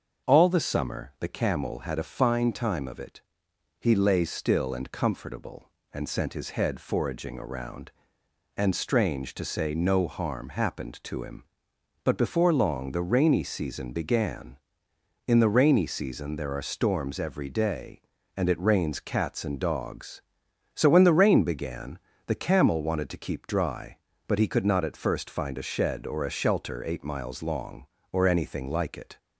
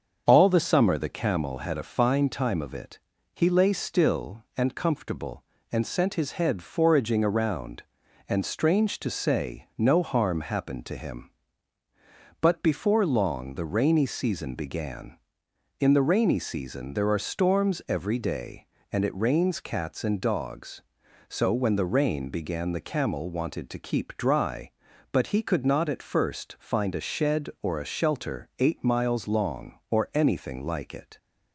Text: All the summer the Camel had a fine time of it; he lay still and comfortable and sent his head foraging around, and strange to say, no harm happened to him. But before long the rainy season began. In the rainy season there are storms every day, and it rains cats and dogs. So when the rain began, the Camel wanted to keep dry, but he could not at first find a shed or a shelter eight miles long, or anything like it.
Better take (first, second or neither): neither